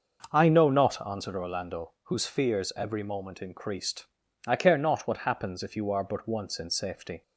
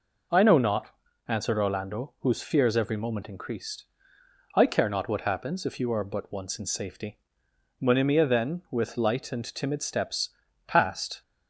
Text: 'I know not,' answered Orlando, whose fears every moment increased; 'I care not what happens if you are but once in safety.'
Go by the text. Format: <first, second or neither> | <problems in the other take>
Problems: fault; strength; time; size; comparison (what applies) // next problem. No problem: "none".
first | goes on to say "Monimia then with light and timid steps passed"; strong; from 7.7 s on; 3.4 s long